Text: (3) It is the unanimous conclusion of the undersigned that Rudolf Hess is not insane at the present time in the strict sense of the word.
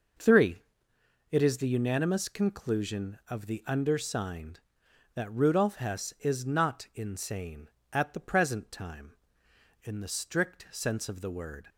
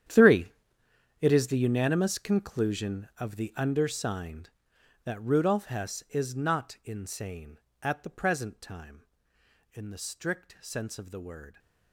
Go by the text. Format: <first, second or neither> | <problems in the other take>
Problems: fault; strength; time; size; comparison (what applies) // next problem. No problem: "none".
first | gets quieter; strong; throughout; 16 dB